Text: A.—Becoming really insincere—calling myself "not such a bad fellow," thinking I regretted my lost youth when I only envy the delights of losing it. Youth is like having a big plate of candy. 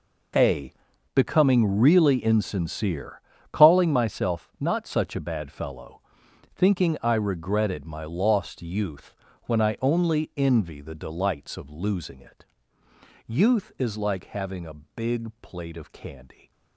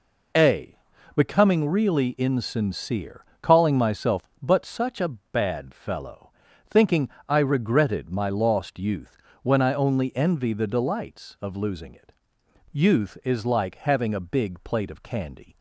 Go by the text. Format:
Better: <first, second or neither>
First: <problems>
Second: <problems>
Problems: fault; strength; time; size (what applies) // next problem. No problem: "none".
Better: first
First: pauses between "youth" and "when"; slight; at 9.1 s; 0.30 s long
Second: says "but" for "not"; at 4.4 s // pauses between "thinking" and "I"; slight; at 7.0 s; 0.18 s long // pauses between "youth" and "when"; slight; at 9.1 s; 0.24 s long